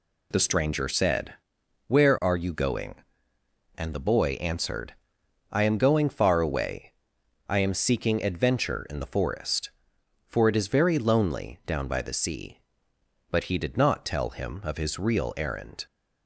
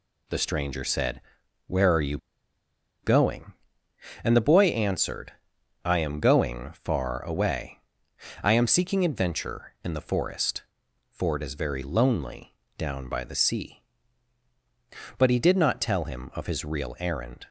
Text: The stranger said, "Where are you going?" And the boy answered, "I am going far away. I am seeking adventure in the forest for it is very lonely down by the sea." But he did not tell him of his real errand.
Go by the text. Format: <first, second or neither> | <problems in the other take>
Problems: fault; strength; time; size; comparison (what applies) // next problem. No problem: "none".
first | pauses between "you" and "going"; noticeable; at 2.1 s; 0.86 s long // pauses between "lonely" and "down"; slight; at 12.5 s; 0.22 s long